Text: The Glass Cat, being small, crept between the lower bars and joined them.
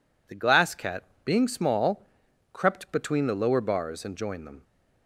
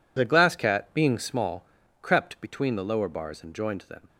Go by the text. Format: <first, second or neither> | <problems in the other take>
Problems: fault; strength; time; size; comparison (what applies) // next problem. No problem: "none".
neither | none